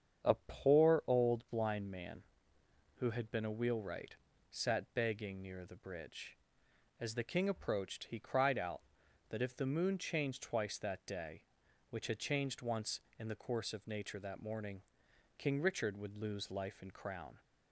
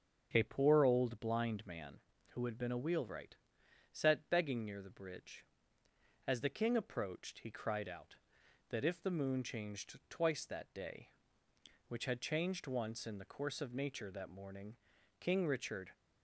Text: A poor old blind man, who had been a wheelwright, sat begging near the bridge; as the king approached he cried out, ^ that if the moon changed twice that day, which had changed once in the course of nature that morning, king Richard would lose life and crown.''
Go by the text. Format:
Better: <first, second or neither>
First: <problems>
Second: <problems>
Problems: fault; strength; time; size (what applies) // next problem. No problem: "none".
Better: first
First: starts louder than the rest; strong; until 1.4 s; 7.5 dB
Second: starts louder than the rest; until 1.3 s; 7 dB // stops before "would lose life and crown"; at 15.9 s